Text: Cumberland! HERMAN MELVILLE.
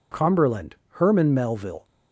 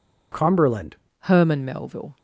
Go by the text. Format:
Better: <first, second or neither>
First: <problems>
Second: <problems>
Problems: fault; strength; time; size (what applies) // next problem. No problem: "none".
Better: first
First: none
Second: changes voice at "HERMAN"; from 1.1 s on; 1.0 s long